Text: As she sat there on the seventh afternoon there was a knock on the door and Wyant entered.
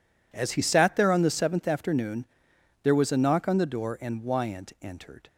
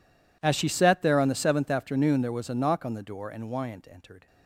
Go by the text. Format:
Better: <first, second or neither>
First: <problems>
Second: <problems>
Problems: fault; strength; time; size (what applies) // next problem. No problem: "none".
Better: second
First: says "he" for "she"; at 0.5 s // pauses between "afternoon" and "there"; noticeable; at 2.2 s; 0.58 s long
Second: none